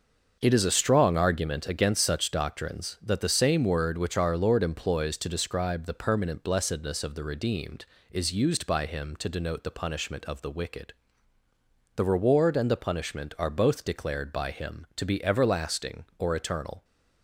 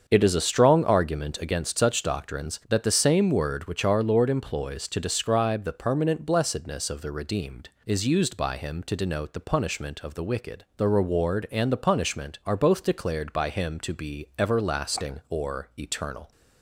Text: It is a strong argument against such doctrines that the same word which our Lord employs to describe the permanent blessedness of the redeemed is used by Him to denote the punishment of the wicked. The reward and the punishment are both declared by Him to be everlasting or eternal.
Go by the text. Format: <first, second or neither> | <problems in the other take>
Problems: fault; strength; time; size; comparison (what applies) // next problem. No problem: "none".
neither | starts louder than the rest; the same in both